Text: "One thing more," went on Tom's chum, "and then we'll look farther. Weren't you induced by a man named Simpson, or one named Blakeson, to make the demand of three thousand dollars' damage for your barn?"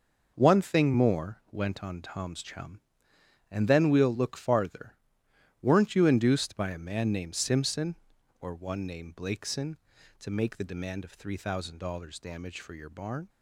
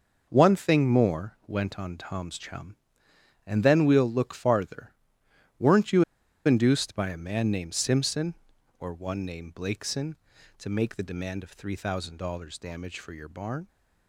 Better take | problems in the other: first | pauses between "you" and "induced"; at 6.0 s; 0.44 s long

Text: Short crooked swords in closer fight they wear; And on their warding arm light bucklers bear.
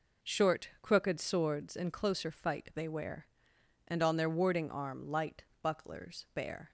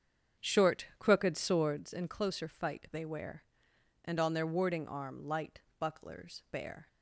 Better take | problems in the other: first | starts louder than the rest; strong; until 1.9 s; 7.5 dB // pauses between "light" and "bucklers"; slight; at 5.6 s; 0.18 s long; slight in the first

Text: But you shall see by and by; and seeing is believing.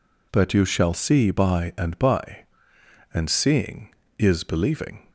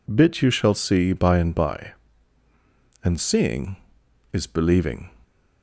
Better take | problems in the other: first | says "Bit" for "But"; at 0.1 s

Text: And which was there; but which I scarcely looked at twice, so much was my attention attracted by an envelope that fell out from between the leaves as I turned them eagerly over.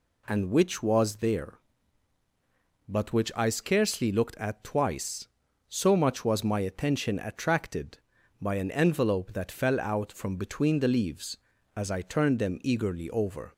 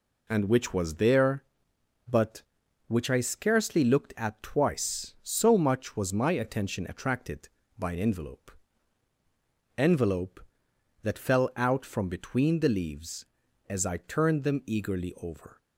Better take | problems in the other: first | says "envelope" twice; at 9.7 s

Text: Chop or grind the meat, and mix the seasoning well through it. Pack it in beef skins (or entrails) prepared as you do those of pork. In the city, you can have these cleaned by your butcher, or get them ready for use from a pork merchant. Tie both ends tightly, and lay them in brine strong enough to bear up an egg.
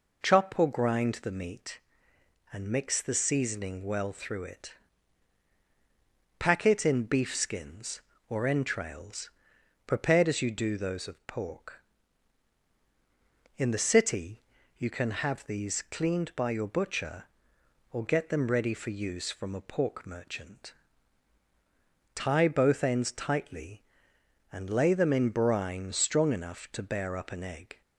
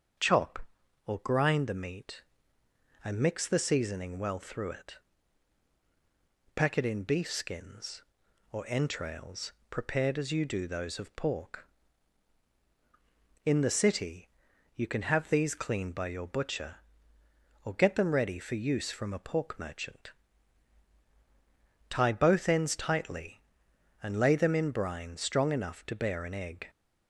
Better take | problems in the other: first | starts louder than the rest; strong; until 1.6 s; 7 dB // skips "up"; at 26.2 s

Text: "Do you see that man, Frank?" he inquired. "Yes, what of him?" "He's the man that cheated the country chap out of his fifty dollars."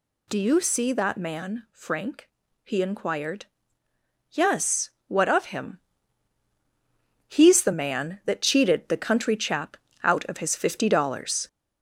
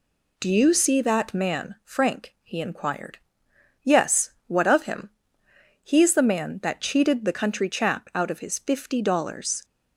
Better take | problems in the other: second | gets louder; throughout; 3.5 dB // pauses between "chap" and "out"; slight; at 9.7 s; 0.26 s long

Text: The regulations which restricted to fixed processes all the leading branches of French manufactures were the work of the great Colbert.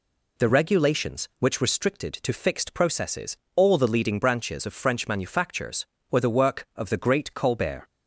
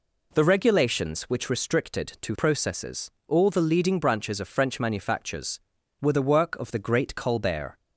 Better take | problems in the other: first | skips "fixed"; at 2.3 s // pauses between "processes" and "all"; slight; at 3.0 s; 0.20 s long; slight in the first

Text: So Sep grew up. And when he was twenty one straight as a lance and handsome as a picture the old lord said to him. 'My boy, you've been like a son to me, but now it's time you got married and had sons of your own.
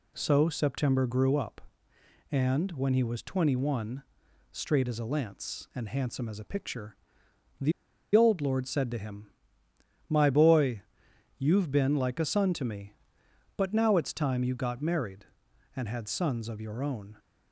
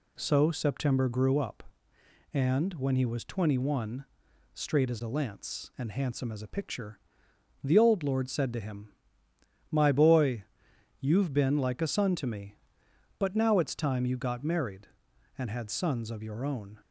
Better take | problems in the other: second | pauses between "one" and "straight"; noticeable; at 4.0 s; 0.50 s long; noticeable in the second // pauses between "picture" and "the"; noticeable; at 6.9 s; 0.66 s long; noticeable in the second // pauses between "the" and "old"; at 7.7 s; 0.43 s long

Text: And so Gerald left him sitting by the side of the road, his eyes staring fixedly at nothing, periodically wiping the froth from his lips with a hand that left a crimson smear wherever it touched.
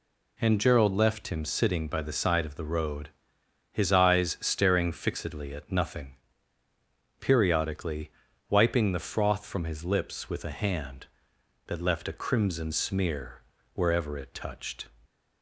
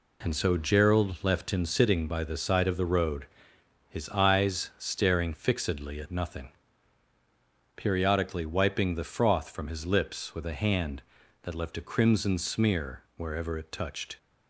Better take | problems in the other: second | skips "so"; at 0.6 s // pauses between "periodically" and "wiping"; at 8.1 s; 0.38 s long // pauses between "smear" and "wherever"; slight; at 13.4 s; 0.32 s long; slight in the second

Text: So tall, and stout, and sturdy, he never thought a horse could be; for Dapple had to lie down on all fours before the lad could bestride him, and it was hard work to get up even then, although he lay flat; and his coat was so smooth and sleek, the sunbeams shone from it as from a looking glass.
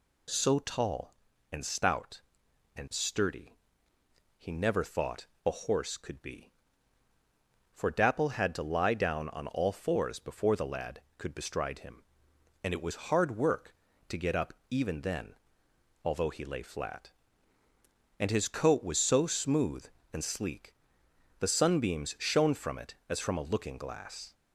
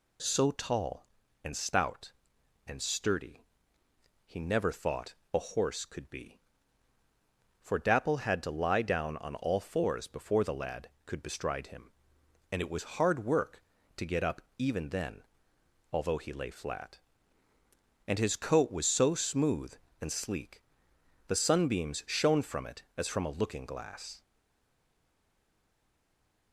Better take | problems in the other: first | pauses between "thought" and "a"; slight; at 5.1 s; 0.18 s long; slight in the first // pauses between "up" and "even"; slight; at 14.4 s; 0.16 s long; slight in the first // stays silent after the last word; from 24.2 s on; 2.3 s long

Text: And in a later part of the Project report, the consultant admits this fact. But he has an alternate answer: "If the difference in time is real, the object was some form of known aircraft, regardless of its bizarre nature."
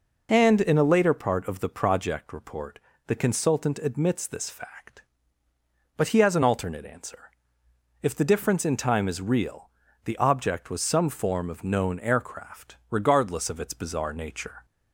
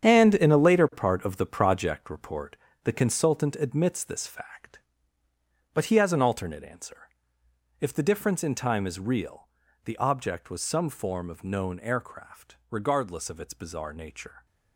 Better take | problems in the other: first | gets quieter; strong; throughout; 11 dB

